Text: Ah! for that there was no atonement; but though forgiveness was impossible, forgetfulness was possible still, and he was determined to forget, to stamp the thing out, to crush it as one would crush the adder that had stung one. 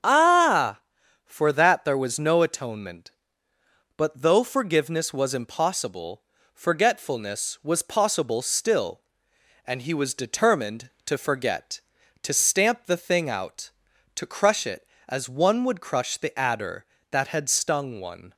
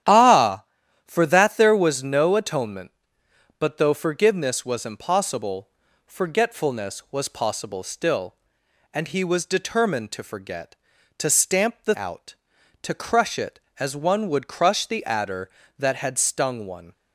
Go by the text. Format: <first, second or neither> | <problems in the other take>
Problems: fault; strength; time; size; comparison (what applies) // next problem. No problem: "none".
first | starts louder than the rest; strong; until 1.4 s; 10.5 dB; strong in the first // skips "thing"; at 11.9 s